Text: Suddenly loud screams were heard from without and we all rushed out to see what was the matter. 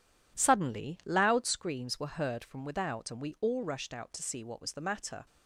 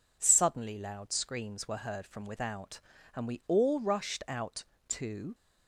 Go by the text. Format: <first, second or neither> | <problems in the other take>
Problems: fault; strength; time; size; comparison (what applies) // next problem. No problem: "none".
first | stops before "see what was the matter"; at 5.3 s